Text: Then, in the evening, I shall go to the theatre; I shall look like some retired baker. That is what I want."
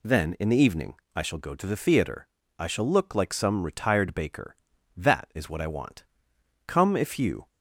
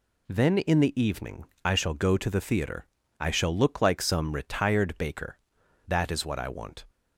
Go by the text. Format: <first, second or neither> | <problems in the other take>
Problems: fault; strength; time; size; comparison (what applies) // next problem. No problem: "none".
second | goes on to say "Come if you"; noticeable; from 6.6 s on; 0.82 s long